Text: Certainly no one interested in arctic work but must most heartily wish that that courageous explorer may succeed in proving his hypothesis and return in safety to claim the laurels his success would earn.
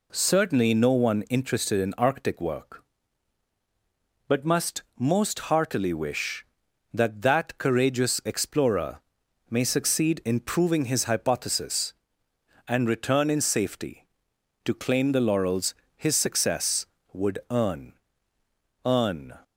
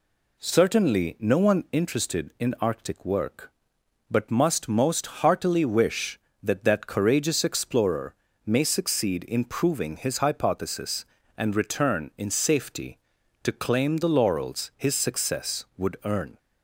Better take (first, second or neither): second